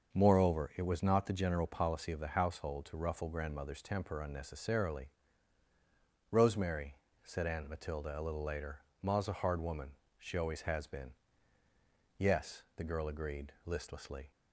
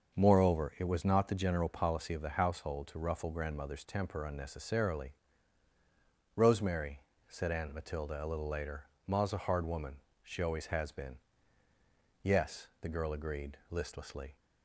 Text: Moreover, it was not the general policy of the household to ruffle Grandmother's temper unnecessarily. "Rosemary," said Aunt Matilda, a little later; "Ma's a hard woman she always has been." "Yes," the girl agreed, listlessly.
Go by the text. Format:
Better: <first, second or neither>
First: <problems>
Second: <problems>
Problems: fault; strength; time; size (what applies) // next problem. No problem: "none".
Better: neither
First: starts louder than the rest; until 1.1 s; 6.5 dB // pauses between "woman" and "she"; slight; at 9.9 s; 0.22 s long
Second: starts louder than the rest; until 1.1 s; 6.5 dB // pauses between "woman" and "she"; slight; at 10.0 s; 0.22 s long